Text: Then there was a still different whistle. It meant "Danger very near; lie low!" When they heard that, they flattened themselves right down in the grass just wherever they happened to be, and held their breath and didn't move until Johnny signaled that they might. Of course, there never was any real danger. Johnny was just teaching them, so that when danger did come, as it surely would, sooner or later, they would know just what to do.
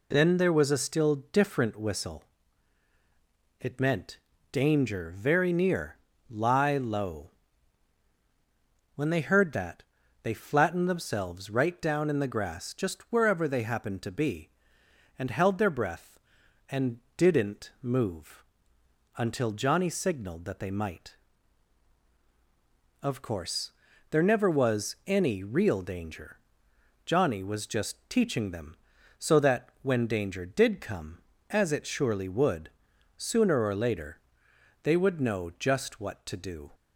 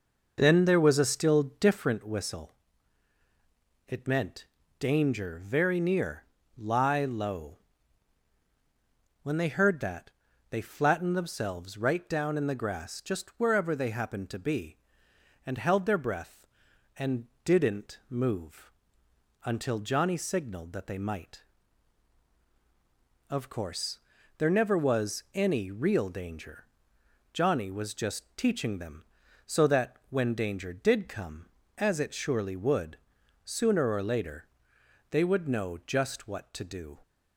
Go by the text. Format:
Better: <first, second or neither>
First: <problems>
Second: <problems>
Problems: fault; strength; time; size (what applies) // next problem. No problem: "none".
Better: first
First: pauses between "meant" and "Danger"; slight; at 4.1 s; 0.34 s long // pauses between "and" and "didn't"; slight; at 16.9 s; 0.18 s long // pauses between "move" and "until"; noticeable; at 18.4 s; 0.72 s long // pauses between "that" and "when"; slight; at 29.6 s; 0.16 s long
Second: starts louder than the rest; noticeable; until 1.9 s; 5.5 dB // pauses between "meant" and "Danger"; slight; at 4.4 s; 0.34 s long // pauses between "and" and "didn't"; slight; at 17.2 s; 0.18 s long // pauses between "move" and "until"; noticeable; at 18.7 s; 0.72 s long // pauses between "that" and "when"; slight; at 29.9 s; 0.16 s long